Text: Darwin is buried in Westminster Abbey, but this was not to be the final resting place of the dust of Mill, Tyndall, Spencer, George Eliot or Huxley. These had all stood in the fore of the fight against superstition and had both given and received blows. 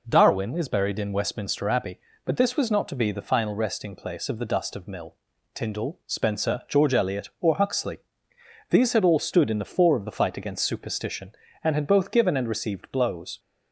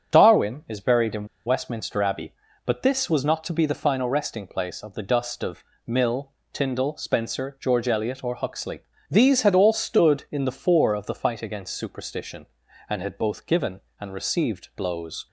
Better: first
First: none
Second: starts louder than the rest; strong; until 1.1 s; 8 dB // pauses between "in" and "Westminster"; slight; at 1.2 s; 0.19 s long // pauses between "of" and "Mill"; slight; at 5.6 s; 0.22 s long

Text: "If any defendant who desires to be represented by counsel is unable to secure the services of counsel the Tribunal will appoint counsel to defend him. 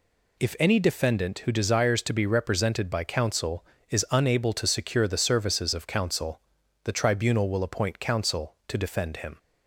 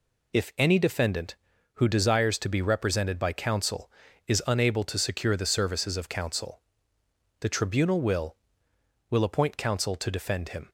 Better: first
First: pauses between "counsel" and "the"; at 6.3 s; 0.44 s long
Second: pauses between "counsel" and "the"; noticeable; at 6.5 s; 0.80 s long // says "will" twice; at 9.0 s

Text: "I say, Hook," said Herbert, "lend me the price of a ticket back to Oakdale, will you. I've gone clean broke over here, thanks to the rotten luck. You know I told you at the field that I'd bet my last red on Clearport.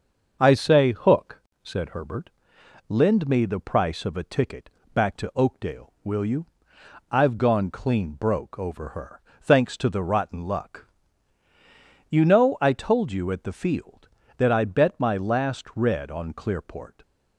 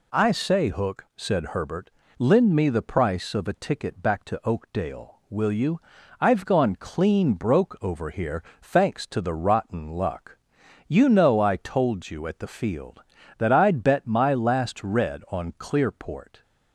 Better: second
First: starts louder than the rest; until 1.4 s; 6.5 dB // pauses between "ticket" and "back"; slight; at 4.6 s; 0.24 s long // says "her" for "here"; at 8.8 s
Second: none

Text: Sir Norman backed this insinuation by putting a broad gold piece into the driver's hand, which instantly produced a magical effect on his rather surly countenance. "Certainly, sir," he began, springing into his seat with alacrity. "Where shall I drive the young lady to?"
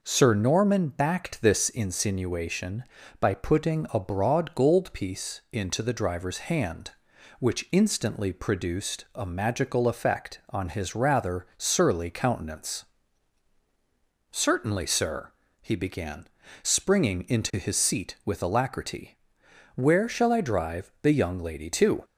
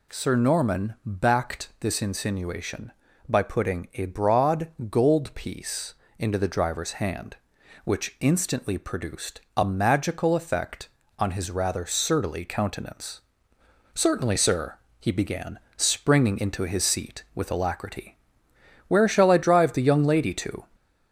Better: first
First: none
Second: gets louder; slight; throughout; 2.5 dB // pauses between "broad" and "gold"; slight; at 4.6 s; 0.20 s long // pauses between "piece" and "into"; slight; at 5.9 s; 0.24 s long // pauses between "produced" and "a"; slight; at 9.3 s; 0.16 s long

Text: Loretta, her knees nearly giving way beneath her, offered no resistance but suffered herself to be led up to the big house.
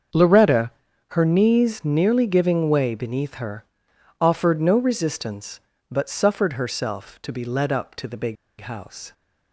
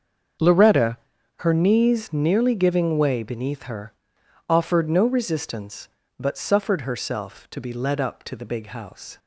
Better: second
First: starts louder than the rest; until 1.5 s; 6.5 dB // pauses between "big" and "house"; slight; at 8.3 s; 0.25 s long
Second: starts louder than the rest; until 1.8 s; 6.5 dB

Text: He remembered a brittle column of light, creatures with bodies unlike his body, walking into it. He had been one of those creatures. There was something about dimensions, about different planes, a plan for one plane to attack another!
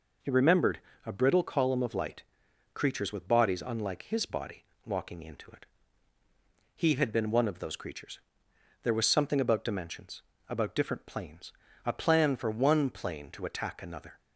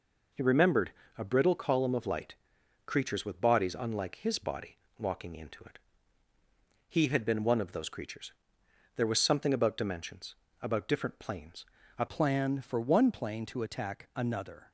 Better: first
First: pauses between "remembered" and "a"; slight; at 0.8 s; 0.26 s long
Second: pauses between "remembered" and "a"; slight; at 0.9 s; 0.26 s long // changes voice at "plan"; from 12.0 s on; 2.7 s long

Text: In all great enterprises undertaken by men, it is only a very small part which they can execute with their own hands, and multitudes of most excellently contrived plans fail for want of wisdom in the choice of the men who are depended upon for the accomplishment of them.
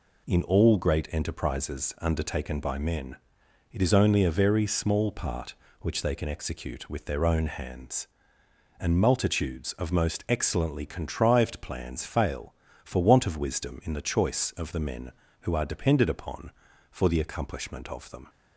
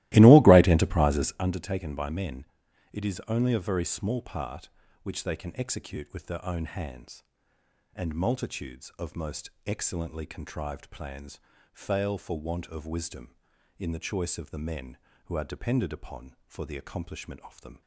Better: first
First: none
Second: starts louder than the rest; strong; until 1.5 s; 17 dB // pauses between "most" and "excellently"; slight; at 9.4 s; 0.16 s long // pauses between "plans" and "fail"; slight; at 11.3 s; 0.34 s long

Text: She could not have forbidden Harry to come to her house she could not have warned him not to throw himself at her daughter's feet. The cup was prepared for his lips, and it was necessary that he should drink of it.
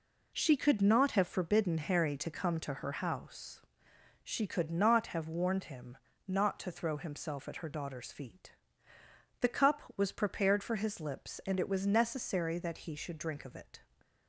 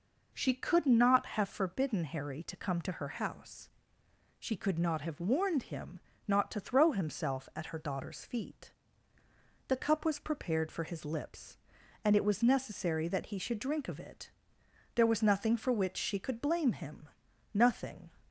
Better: first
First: pauses between "house" and "she"; noticeable; at 3.6 s; 0.64 s long // pauses between "him" and "not"; slight; at 5.9 s; 0.32 s long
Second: pauses between "house" and "she"; noticeable; at 3.6 s; 0.70 s long // pauses between "him" and "not"; slight; at 6.0 s; 0.26 s long // goes on to say "There was nothing for which she could blame him nothing"; strong; from 14.9 s on; 3.1 s long

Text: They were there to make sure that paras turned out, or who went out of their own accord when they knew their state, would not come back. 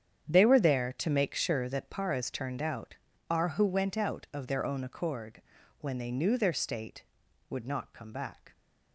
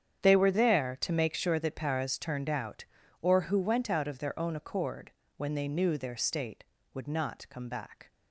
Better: second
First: starts louder than the rest; strong; until 1.3 s; 8.5 dB // says "are" for "or"; at 3.2 s // pauses between "accord" and "when"; at 5.4 s; 0.40 s long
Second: starts louder than the rest; strong; until 1.2 s; 8.5 dB // pauses between "accord" and "when"; slight; at 5.1 s; 0.26 s long

